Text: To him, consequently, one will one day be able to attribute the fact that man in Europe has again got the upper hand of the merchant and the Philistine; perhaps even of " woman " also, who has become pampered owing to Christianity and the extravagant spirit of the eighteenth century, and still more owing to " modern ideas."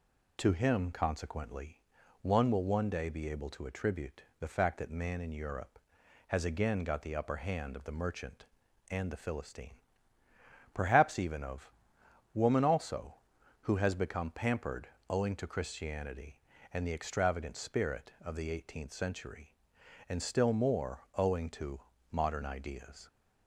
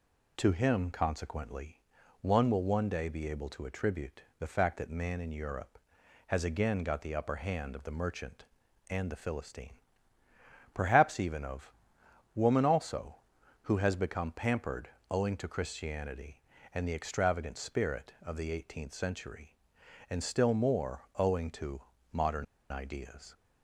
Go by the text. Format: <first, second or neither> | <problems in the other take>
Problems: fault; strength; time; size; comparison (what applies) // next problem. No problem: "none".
first | pauses between "attribute" and "the"; slight; at 4.2 s; 0.16 s long; slight in the first // pauses between "pampered" and "owing"; slight; at 14.8 s; 0.20 s long; slight in the first // pauses between "modern" and "ideas"; slight; at 22.4 s; 0.26 s long